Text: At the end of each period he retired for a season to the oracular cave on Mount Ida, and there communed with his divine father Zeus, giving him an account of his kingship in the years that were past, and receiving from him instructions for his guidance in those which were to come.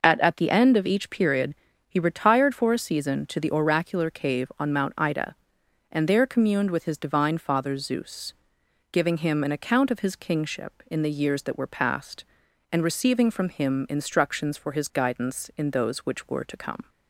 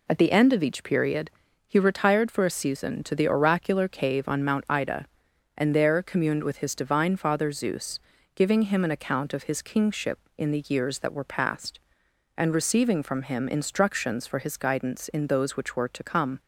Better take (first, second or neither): second